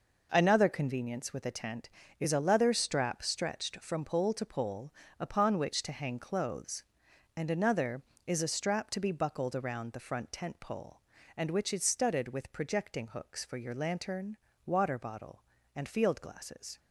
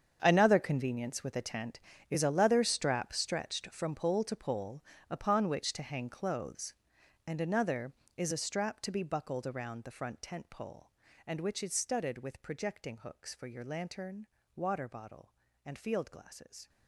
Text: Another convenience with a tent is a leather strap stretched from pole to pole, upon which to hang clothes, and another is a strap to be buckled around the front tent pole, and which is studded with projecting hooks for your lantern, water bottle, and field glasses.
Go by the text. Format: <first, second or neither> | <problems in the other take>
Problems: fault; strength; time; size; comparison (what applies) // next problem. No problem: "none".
first | gets quieter; strong; throughout; 15 dB